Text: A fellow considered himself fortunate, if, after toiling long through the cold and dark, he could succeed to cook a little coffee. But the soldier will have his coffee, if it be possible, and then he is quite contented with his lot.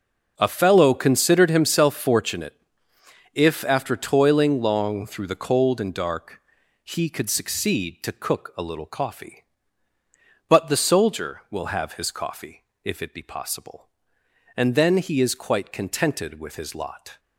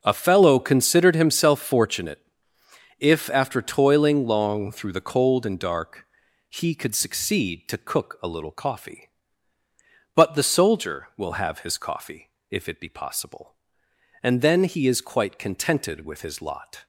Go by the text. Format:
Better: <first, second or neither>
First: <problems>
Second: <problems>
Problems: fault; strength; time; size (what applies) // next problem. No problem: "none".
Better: neither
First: none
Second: none